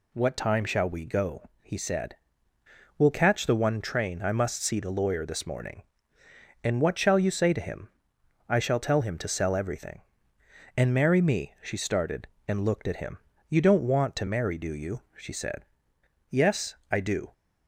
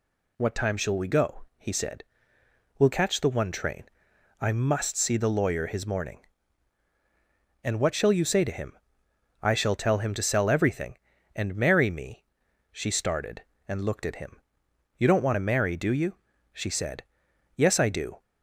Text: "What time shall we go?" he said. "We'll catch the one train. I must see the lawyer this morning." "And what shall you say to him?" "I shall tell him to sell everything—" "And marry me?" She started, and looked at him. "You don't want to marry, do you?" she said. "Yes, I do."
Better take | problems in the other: first | says "his" for "this"; at 5.6 s

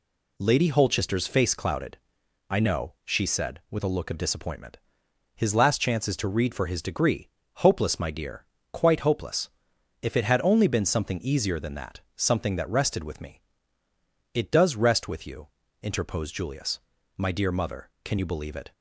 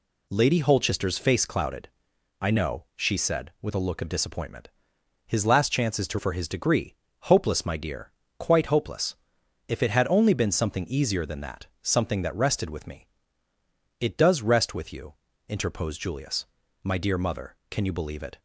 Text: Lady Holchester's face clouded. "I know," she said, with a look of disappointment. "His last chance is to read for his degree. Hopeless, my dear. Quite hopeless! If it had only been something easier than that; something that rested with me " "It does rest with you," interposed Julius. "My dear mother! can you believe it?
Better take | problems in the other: first | skips "read"; at 6.1 s

